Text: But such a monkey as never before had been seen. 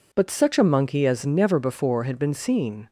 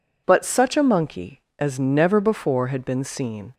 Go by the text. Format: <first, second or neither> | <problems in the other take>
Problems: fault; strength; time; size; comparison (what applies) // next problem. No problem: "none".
neither | none